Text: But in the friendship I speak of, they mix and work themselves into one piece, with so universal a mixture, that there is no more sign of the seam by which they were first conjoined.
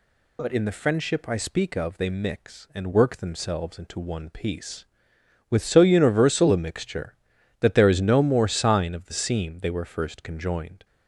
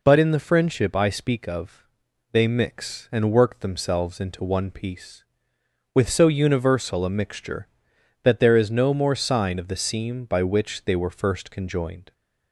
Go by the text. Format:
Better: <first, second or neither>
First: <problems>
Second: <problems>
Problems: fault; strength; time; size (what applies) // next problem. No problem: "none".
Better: second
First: skips "by which"; at 9.6 s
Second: none